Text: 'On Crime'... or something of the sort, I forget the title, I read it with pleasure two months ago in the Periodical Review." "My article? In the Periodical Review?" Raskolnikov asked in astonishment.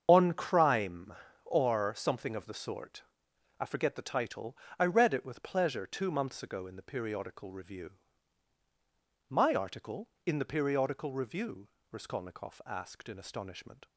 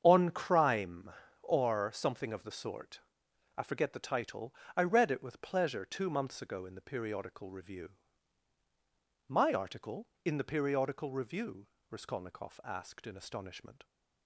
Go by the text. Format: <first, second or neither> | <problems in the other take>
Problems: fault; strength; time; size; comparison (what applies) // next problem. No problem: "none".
second | loses the start of "On"; at 0.0 s; 25 ms // starts louder than the rest; strong; until 1.0 s; 7 dB; strong in the second